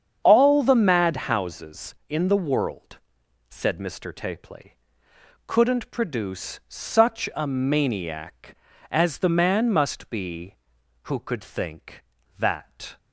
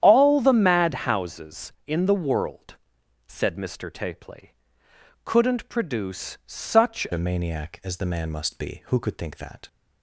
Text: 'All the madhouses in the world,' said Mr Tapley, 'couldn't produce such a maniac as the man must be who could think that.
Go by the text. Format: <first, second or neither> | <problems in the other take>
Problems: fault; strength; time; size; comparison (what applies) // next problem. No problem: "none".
first | starts louder than the rest; strong; until 1.0 s; 10 dB; strong in the first // changes voice at "a"; from 7.1 s on; 2.5 s long